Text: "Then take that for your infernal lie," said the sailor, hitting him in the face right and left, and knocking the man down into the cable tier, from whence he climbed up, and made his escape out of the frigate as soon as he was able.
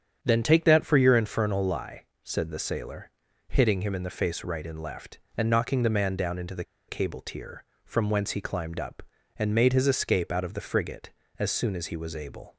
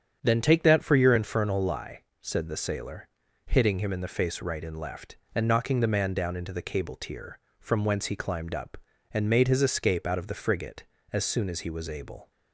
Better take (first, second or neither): second